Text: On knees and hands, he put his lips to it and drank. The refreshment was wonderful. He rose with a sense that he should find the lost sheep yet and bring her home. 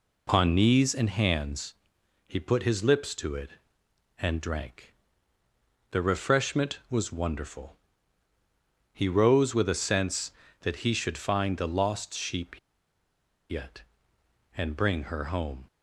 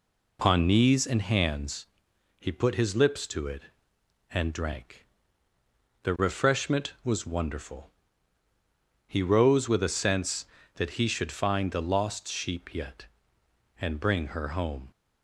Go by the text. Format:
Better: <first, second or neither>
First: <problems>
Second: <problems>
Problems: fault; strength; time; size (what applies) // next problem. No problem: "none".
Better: second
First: pauses between "sheep" and "yet"; noticeable; at 12.5 s; 0.91 s long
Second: none